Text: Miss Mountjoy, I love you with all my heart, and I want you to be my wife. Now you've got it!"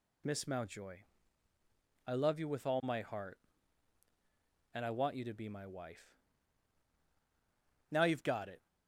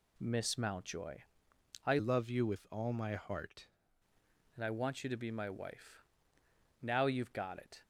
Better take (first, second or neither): first